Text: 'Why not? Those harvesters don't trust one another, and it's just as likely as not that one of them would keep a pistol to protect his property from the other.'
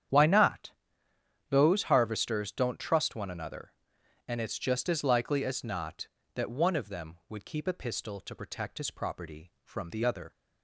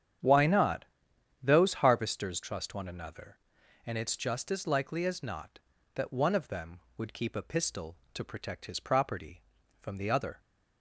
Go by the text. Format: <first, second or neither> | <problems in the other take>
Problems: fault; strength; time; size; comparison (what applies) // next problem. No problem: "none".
first | starts louder than the rest; strong; until 1.8 s; 8.5 dB; strong in the first // skips "don't"; at 2.4 s